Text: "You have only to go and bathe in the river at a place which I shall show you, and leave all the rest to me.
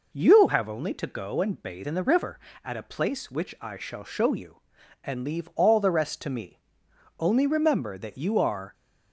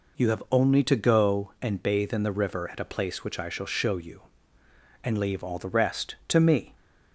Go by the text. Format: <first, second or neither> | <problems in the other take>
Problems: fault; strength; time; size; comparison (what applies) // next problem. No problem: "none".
second | goes on to say "Only remember that you are"; from 7.1 s on; 1.5 s long